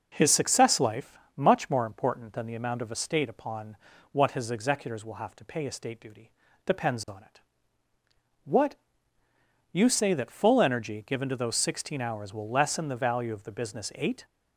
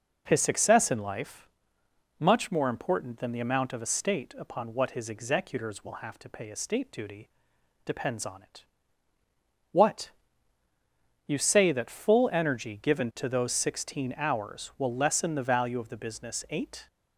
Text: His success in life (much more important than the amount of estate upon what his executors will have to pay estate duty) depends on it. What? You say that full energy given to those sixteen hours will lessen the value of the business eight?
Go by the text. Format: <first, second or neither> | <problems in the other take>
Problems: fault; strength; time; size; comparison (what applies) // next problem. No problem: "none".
second | skips "in"; at 0.7 s // pauses between "upon" and "what"; slight; at 3.7 s; 0.34 s long